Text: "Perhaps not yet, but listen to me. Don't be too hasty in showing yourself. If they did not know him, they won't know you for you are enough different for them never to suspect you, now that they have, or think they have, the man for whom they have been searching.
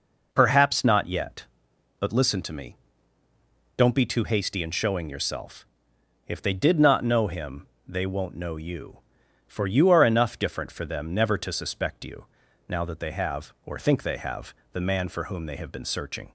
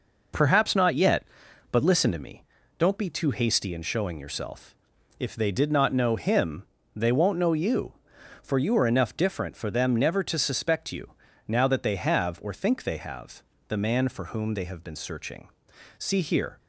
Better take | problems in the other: first | goes on to say "See here"; noticeable; from 15.9 s on; 0.62 s long

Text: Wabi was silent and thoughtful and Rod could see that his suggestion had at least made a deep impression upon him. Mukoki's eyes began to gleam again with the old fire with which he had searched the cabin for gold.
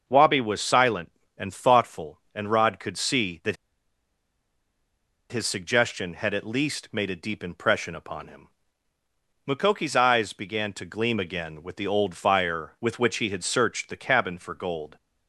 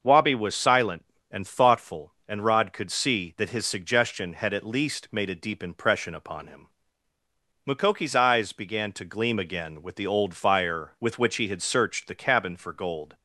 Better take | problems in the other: second | starts louder than the rest; until 1.0 s; 6.5 dB; also in the second // pauses between "that" and "his"; strong; at 3.5 s; 1.7 s long

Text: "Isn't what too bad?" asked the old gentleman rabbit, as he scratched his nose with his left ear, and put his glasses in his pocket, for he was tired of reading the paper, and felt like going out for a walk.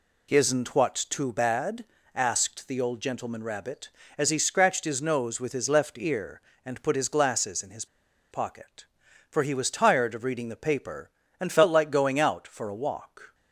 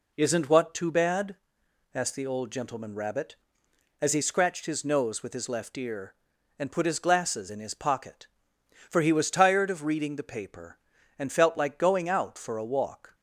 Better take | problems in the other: second | pauses between "what" and "too"; slight; at 0.9 s; 0.16 s long // pauses between "his" and "pocket"; noticeable; at 7.8 s; 0.45 s long

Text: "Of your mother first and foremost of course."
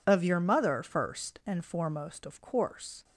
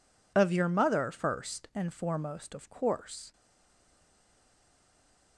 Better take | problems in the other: first | stays silent after the last word; noticeable; from 3.3 s on; 2.0 s long

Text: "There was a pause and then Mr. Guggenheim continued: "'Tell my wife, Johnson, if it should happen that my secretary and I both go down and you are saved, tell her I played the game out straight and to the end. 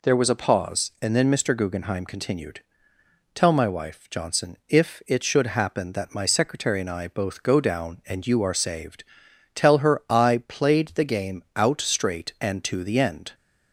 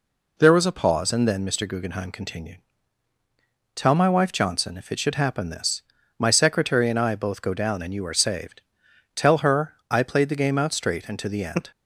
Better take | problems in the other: first | says "this" for "that"; at 5.4 s

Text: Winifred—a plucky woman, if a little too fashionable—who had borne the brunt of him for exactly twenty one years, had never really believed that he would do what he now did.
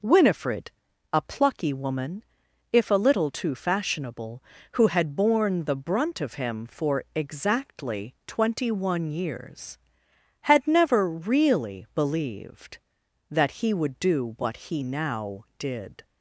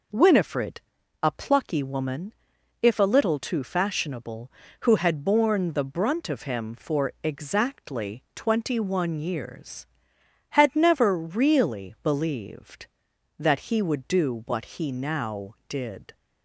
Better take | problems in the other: neither | none

